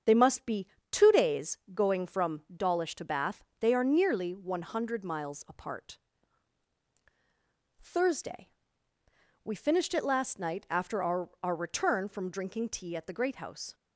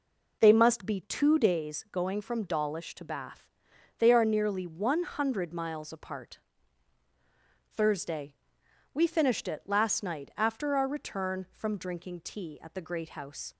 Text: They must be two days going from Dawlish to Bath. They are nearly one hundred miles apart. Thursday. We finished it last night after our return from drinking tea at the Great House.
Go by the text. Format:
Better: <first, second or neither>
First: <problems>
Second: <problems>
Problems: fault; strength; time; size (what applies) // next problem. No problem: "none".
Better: second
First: starts louder than the rest; strong; until 1.3 s; 8 dB // pauses between "be" and "two"; slight; at 0.6 s; 0.24 s long // says "our" twice; at 11.4 s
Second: none